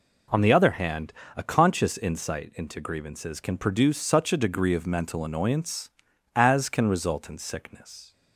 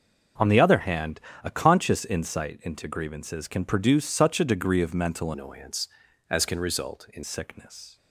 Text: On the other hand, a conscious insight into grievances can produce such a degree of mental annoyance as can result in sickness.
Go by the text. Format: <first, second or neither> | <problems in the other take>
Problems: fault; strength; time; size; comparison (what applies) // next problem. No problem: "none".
first | changes voice from "annoyance" to "in"; from 5.3 to 7.2 s; 1.9 s long